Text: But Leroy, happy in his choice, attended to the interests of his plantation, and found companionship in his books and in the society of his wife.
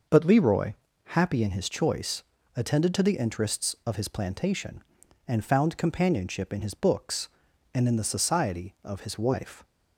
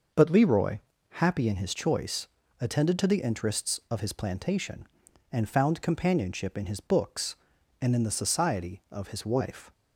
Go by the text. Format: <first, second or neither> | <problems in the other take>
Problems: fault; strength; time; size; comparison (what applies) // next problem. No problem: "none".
neither | none